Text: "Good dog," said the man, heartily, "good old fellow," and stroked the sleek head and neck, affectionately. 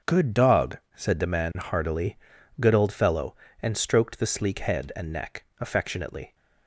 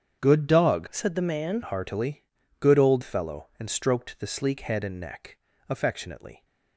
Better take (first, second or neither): first